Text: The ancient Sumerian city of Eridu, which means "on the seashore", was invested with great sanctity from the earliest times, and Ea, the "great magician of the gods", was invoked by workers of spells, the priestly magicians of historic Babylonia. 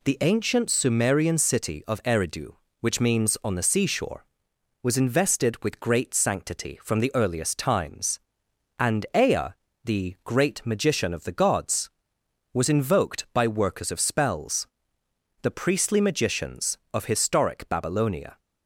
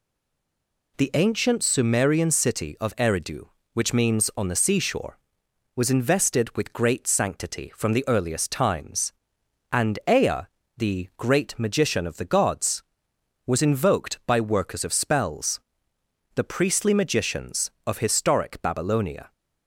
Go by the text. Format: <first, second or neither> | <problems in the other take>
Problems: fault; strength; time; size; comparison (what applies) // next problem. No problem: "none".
first | stays silent before the first word; slight; until 0.9 s; 0.9 s long